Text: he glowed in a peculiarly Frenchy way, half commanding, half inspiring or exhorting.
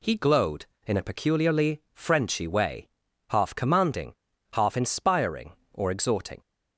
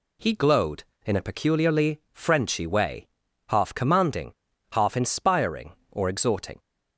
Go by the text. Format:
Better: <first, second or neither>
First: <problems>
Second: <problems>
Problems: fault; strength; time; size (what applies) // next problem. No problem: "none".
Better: neither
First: none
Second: none